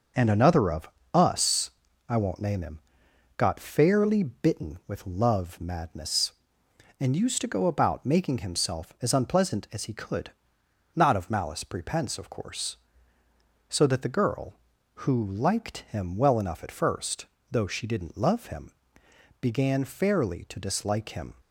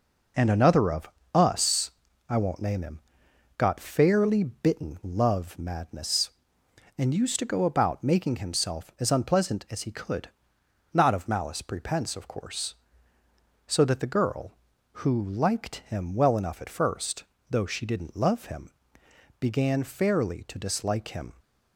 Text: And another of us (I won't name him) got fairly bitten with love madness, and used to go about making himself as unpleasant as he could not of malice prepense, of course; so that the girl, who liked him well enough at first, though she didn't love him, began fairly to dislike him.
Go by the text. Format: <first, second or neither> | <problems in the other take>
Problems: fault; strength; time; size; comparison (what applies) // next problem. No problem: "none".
first | pauses between "of" and "us"; slight; at 1.0 s; 0.26 s long; slight in the first // skips "with"; at 5.0 s // pauses between "could" and "not"; noticeable; at 10.2 s; 0.64 s long; noticeable in the first